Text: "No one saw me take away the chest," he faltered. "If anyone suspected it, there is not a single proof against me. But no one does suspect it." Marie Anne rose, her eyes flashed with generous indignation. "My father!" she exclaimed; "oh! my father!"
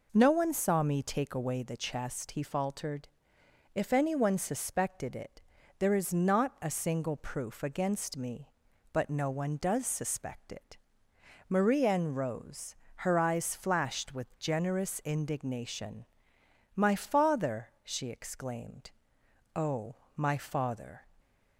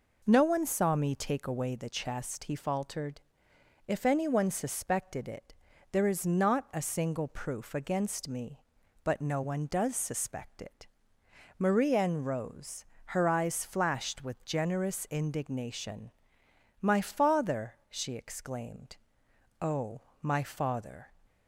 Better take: neither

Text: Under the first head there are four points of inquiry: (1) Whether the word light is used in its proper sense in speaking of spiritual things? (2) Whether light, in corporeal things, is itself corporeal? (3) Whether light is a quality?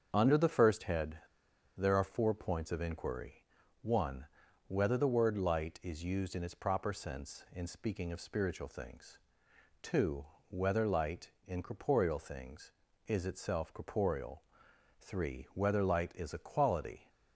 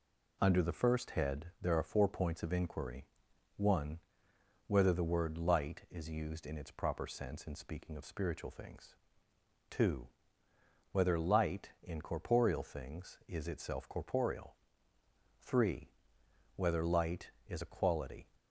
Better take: second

